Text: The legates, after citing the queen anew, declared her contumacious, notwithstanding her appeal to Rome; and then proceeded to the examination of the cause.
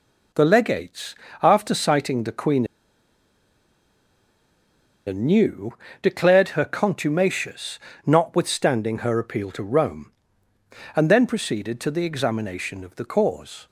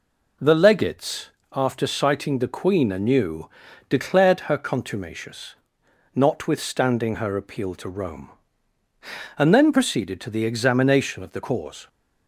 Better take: second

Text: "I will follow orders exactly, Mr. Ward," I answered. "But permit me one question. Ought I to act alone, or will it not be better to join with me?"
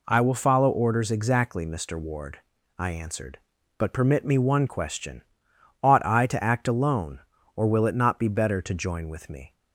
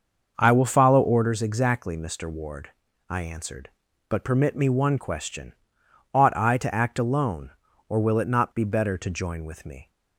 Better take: first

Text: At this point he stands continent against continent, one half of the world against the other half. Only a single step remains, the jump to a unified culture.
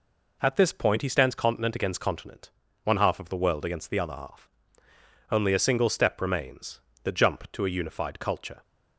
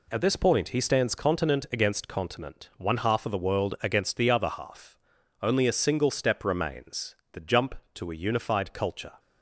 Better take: neither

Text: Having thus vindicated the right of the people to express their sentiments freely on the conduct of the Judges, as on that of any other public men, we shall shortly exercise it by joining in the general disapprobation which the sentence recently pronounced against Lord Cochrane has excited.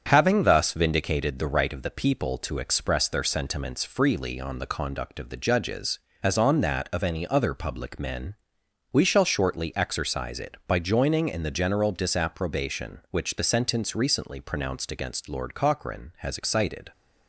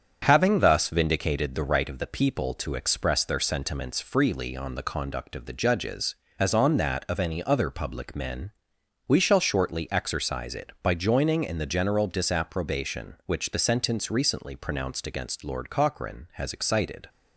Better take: neither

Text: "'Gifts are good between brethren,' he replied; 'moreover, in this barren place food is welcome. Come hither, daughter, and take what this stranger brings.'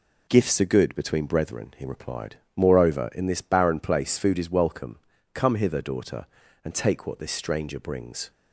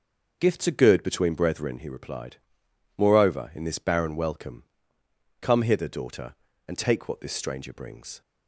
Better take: first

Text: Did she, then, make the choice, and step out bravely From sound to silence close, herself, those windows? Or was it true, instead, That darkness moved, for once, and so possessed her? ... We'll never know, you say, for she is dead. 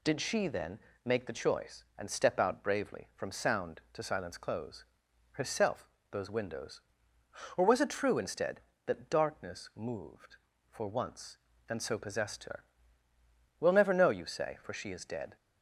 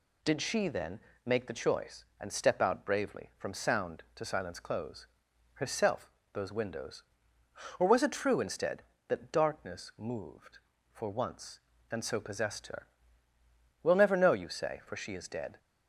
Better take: neither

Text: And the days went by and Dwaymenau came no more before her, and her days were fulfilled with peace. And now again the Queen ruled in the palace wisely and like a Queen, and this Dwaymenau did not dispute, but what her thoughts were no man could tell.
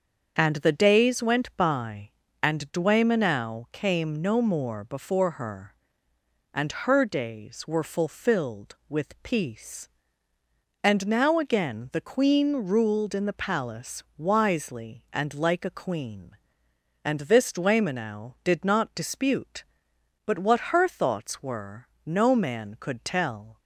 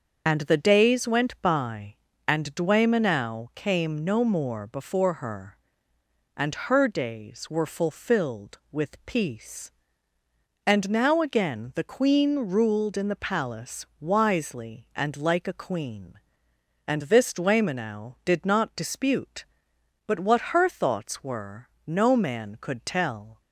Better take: first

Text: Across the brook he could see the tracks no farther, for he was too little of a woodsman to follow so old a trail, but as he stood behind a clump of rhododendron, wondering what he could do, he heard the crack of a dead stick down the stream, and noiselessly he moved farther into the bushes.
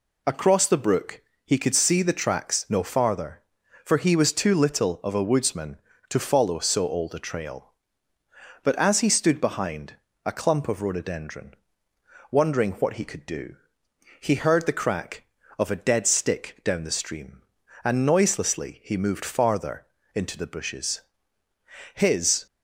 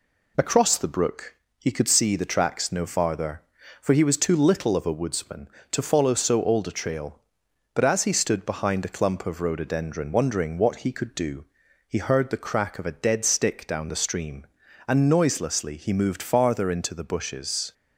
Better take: second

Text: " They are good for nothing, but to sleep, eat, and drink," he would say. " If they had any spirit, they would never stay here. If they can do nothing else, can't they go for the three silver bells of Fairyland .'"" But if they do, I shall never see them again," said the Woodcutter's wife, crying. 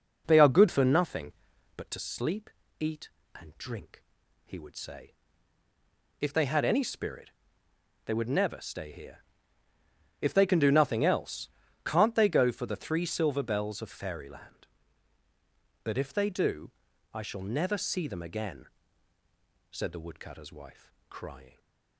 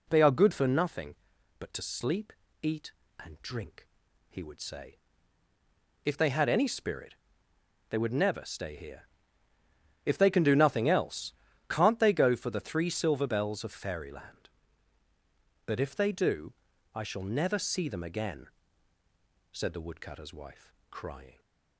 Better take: second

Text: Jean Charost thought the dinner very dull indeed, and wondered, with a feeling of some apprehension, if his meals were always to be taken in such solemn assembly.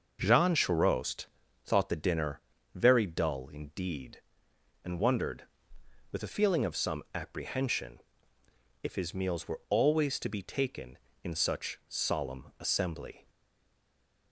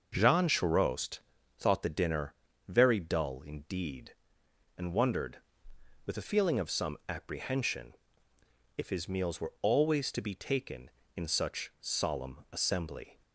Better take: second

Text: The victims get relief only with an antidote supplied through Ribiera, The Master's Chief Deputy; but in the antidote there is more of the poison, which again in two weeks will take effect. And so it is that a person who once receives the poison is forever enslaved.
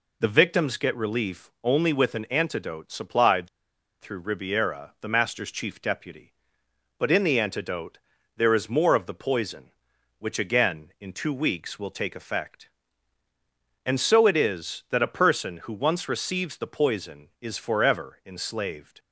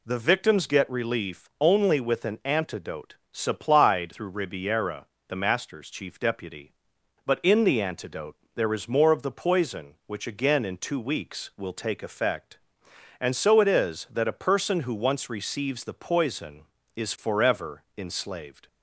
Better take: second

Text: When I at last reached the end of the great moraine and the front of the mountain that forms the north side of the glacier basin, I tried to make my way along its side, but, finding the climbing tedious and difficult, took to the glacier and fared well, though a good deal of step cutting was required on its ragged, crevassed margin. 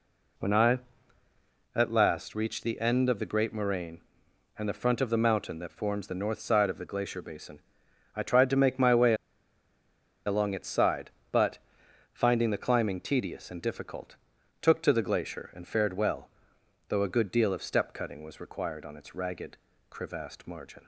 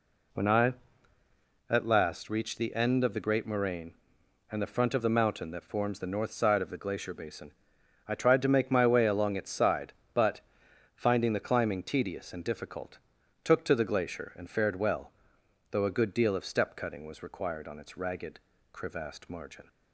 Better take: second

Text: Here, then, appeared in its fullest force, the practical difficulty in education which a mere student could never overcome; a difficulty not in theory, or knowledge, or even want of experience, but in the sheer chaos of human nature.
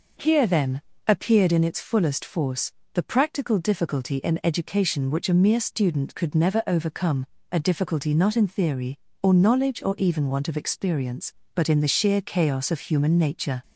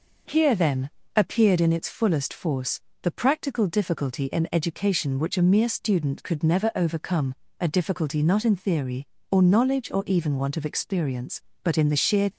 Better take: first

